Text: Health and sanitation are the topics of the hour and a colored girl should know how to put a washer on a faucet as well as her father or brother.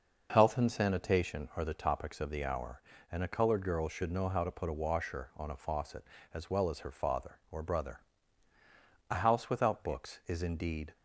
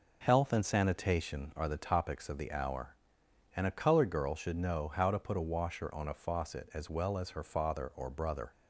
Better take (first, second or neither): second